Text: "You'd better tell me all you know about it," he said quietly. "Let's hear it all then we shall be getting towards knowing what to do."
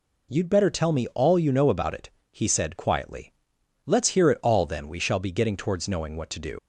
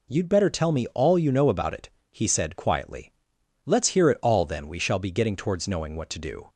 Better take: second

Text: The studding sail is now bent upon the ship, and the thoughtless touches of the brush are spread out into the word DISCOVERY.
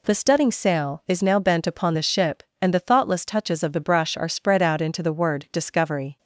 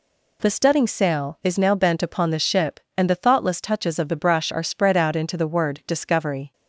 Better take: neither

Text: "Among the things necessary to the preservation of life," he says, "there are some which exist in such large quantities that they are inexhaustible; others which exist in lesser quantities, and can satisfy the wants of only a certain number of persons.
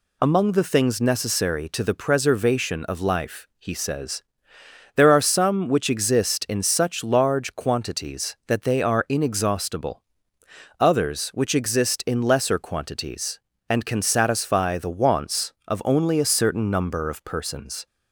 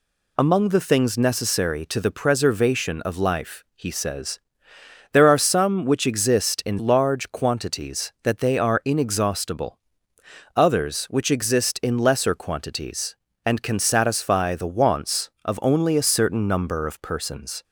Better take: first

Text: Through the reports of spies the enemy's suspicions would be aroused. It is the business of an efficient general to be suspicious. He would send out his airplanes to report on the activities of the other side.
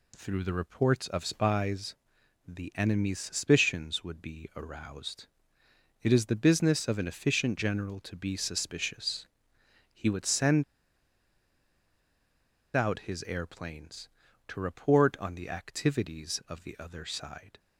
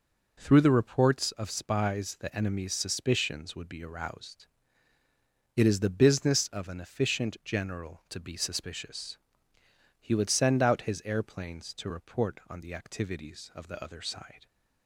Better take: second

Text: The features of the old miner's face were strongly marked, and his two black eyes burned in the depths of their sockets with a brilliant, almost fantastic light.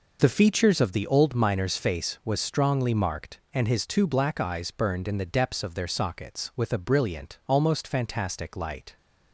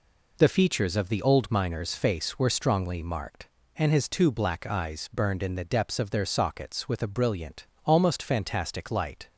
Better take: second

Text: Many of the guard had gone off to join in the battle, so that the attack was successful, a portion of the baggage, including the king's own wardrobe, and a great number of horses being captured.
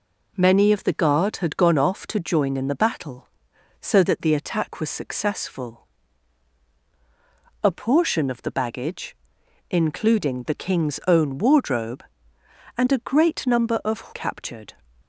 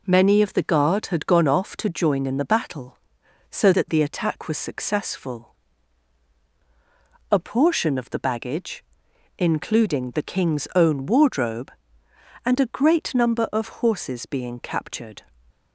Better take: second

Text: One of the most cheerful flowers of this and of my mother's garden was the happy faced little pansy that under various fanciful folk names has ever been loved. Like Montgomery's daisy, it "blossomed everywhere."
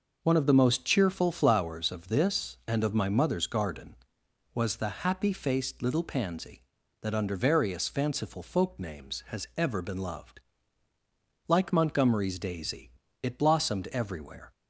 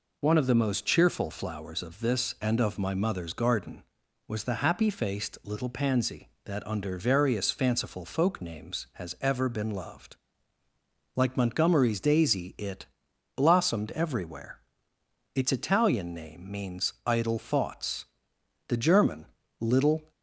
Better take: first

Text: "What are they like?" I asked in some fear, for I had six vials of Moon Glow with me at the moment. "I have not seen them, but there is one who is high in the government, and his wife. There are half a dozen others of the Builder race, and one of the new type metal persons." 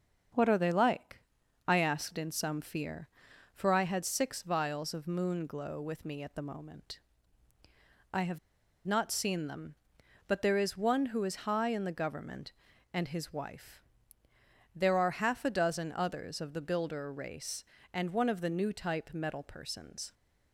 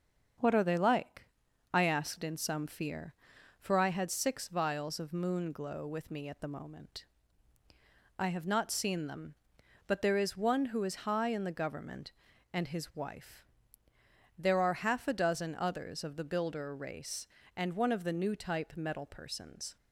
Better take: second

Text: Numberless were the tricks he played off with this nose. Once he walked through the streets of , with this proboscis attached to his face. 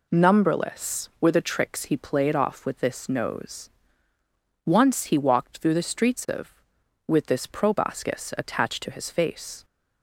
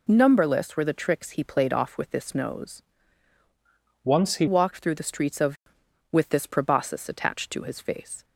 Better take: first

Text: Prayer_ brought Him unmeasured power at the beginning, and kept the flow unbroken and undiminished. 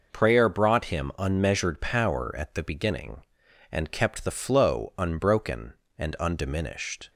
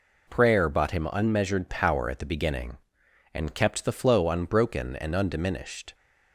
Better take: first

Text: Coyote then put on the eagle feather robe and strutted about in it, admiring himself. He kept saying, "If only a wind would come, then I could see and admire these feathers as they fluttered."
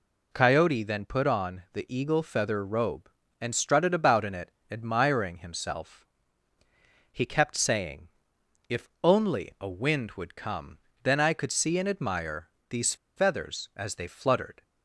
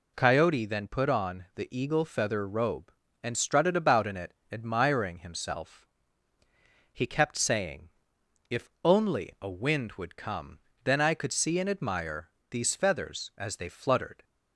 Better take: second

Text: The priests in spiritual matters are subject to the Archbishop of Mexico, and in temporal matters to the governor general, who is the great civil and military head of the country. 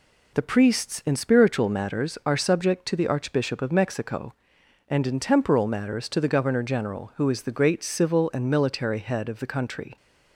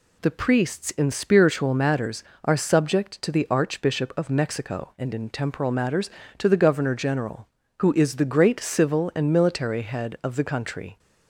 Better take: neither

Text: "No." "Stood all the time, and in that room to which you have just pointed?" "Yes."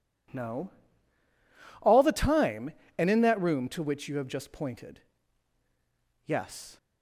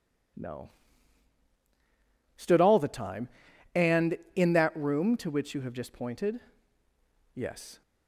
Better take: second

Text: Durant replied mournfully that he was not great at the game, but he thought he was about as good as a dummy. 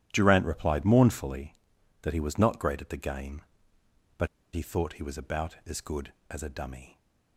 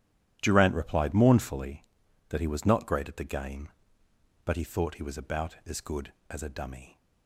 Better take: second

